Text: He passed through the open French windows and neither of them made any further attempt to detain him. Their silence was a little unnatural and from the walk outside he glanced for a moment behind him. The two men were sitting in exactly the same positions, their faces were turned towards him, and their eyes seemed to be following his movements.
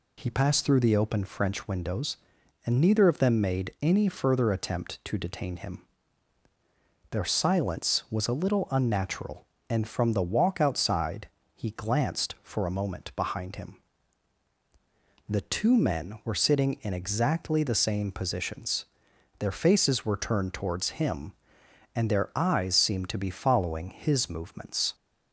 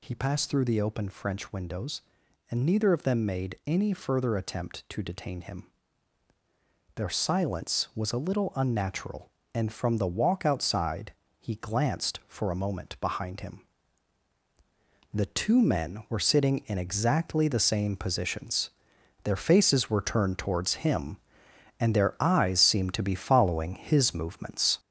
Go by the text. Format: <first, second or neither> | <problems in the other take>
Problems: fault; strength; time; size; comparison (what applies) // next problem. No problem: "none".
first | gets louder; noticeable; throughout; 4.5 dB // pauses between "outside" and "he"; slight; at 11.1 s; 0.26 s long; slight in the first